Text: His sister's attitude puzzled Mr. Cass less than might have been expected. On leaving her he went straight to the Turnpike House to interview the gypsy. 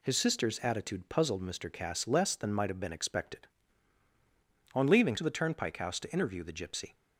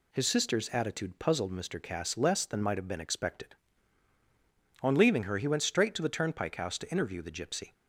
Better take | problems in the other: second | skips "her he went straight"; at 5.1 s

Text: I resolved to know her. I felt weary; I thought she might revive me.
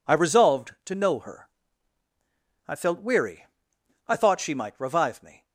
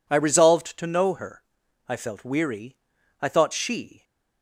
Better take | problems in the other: first | stops before "might revive me"; at 4.0 s

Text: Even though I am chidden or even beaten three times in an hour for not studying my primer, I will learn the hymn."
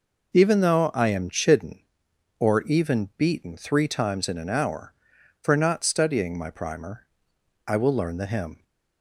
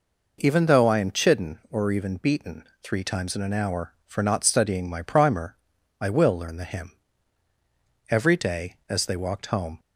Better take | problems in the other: first | pauses between "beaten" and "three"; slight; at 2.6 s; 0.18 s long // goes on to say "Every day as they walked home"; strong; from 8.0 s on; 1.7 s long

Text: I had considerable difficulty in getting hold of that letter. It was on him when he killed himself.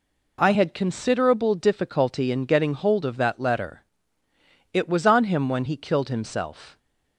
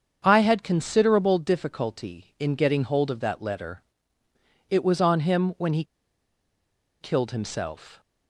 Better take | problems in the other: first | starts louder than the rest; until 1.2 s; 7 dB // pauses between "he" and "killed"; at 5.8 s; 1.1 s long

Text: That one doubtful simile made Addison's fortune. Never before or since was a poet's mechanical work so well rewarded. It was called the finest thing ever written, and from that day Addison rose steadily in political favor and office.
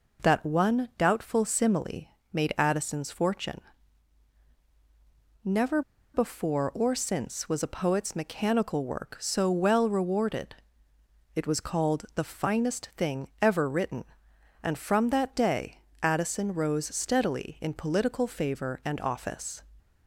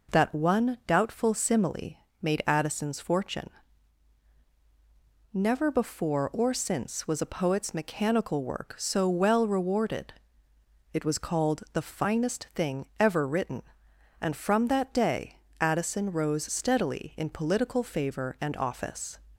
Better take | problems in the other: second | pauses between "simile" and "made"; slight; at 2.0 s; 0.22 s long; slight in the second // pauses between "Never" and "before"; slight; at 5.8 s; 0.33 s long // pauses between "day" and "Addison"; slight; at 15.7 s; 0.24 s long; slight in the second

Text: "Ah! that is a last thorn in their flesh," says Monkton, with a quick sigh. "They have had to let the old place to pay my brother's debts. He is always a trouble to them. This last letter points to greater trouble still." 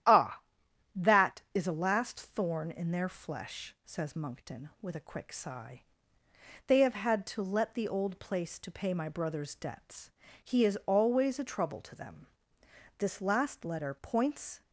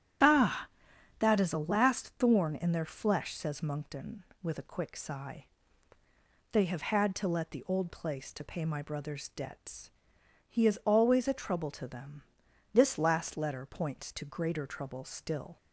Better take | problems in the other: second | starts louder than the rest; strong; until 1.7 s; 11 dB; strong in the second // stops before "to greater trouble still"; at 14.6 s

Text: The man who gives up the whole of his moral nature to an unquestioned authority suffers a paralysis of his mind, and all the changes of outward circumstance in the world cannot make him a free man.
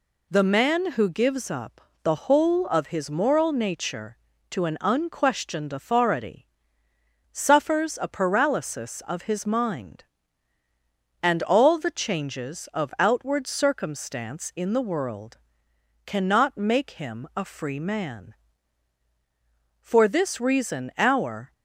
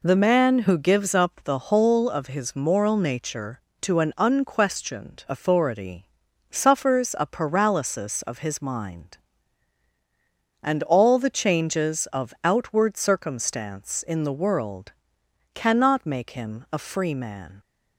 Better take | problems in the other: second | pauses between "up" and "the"; slight; at 1.8 s; 0.22 s long // pauses between "authority" and "suffers"; noticeable; at 6.4 s; 0.86 s long; also in the second // pauses between "world" and "cannot"; noticeable; at 15.3 s; 0.68 s long; noticeable in the second // goes on to say "For this reason our"; strong; from 19.8 s on; 1.7 s long

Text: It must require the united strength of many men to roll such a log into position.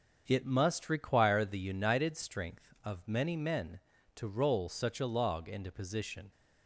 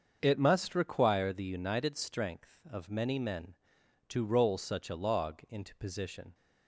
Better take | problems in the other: neither | starts louder than the rest; the same in both

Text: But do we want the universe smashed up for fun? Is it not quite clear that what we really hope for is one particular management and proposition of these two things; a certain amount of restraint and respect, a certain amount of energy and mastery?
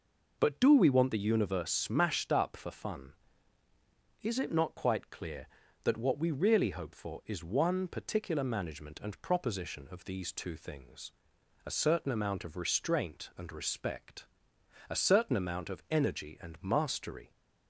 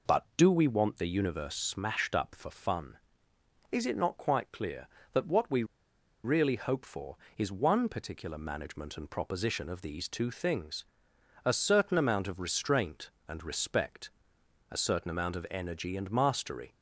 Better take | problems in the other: first | pauses between "we" and "really"; noticeable; at 5.6 s; 0.61 s long

